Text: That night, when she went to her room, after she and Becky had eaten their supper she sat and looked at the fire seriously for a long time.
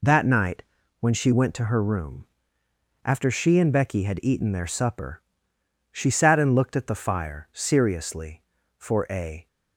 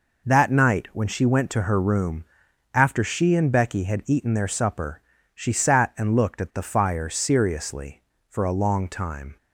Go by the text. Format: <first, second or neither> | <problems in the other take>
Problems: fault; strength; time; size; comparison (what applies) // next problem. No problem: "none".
second | pauses between "supper" and "she"; noticeable; at 5.2 s; 0.70 s long; slight in the second // stops before "long time"; at 9.4 s